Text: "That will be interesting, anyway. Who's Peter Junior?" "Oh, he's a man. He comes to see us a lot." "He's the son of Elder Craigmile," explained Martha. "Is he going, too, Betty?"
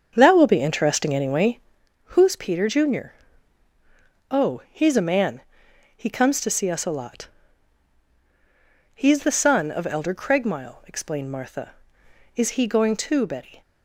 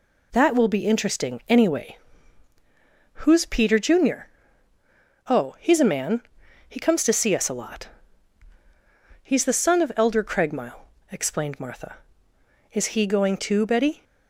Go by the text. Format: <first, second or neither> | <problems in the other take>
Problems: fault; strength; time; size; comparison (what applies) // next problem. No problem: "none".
second | starts louder than the rest; until 1.9 s; 7 dB